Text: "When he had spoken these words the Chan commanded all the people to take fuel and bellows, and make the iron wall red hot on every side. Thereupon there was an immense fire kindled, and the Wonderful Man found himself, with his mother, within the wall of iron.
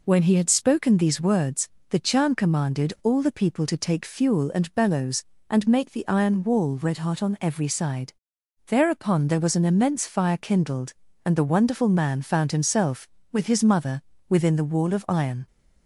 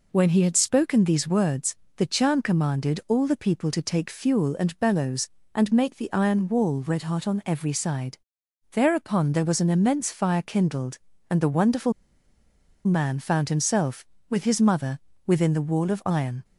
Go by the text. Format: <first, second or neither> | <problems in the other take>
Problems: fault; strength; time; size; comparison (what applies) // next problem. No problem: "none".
first | pauses between "words" and "the"; slight; at 1.7 s; 0.22 s long; slight in the first // pauses between "Wonderful" and "Man"; noticeable; at 11.9 s; 0.93 s long